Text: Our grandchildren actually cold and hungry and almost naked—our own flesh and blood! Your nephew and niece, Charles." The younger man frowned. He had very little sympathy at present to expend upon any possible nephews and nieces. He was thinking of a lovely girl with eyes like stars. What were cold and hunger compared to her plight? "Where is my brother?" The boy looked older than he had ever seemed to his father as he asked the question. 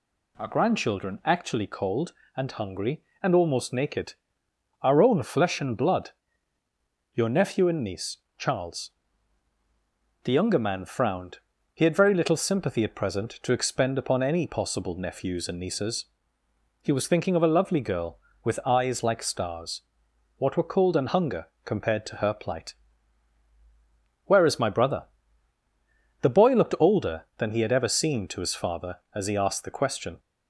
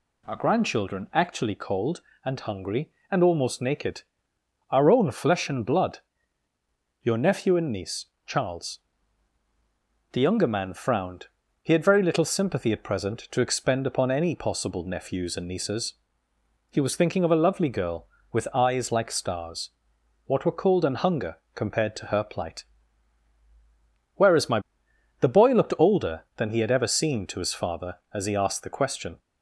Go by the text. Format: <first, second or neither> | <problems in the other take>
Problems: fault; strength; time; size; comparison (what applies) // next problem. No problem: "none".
first | pauses between "hunger" and "compared"; slight; at 21.3 s; 0.18 s long; slight in the first // skips "brother"; at 24.8 s